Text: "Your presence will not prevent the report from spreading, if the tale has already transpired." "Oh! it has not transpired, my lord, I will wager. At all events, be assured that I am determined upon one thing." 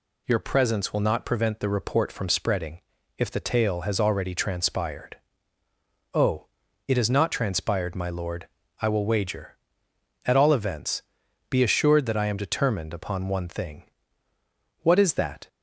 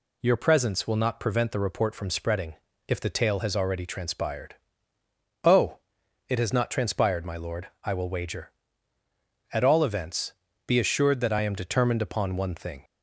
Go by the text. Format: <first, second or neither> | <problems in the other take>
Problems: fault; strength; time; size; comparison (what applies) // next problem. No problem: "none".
second | goes on to say "What is that"; noticeable; from 14.8 s on; 0.66 s long